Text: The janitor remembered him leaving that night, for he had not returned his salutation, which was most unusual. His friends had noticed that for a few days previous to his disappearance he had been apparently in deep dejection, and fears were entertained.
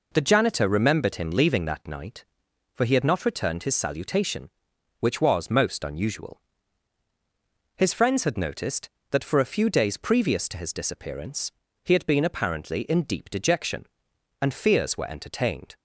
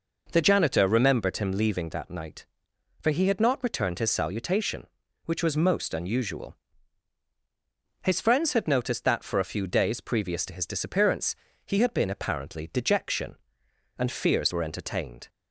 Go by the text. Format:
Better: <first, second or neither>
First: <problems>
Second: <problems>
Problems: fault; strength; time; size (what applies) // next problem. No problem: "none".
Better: first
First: pauses between "disappearance" and "he"; slight; at 11.5 s; 0.32 s long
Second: pauses between "disappearance" and "he"; slight; at 11.3 s; 0.30 s long // skips "in deep"; at 12.7 s